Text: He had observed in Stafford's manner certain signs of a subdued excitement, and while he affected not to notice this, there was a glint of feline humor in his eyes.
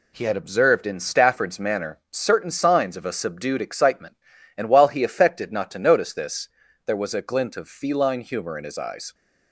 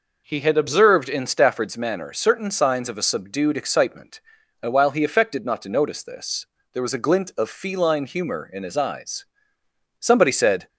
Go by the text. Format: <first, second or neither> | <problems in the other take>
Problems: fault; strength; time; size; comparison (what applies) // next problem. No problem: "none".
first | goes on to say "Somebody said"; noticeable; from 9.9 s on; 0.68 s long